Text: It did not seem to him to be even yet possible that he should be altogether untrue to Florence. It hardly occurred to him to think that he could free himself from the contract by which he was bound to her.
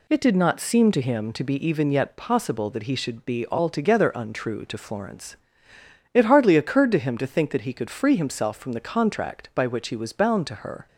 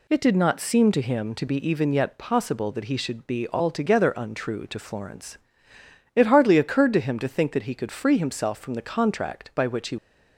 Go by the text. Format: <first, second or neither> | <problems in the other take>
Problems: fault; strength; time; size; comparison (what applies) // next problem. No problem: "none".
first | stops before "was bound to her"; at 9.9 s